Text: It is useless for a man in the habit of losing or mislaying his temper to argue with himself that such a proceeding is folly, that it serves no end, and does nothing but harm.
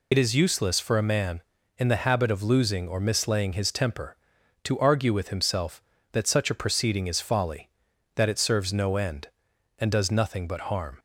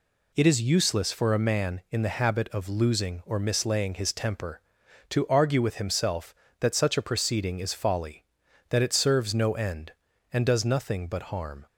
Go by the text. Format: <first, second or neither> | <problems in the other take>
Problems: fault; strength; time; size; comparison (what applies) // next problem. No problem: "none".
second | loses the start of "It"; at 0.1 s; 50 ms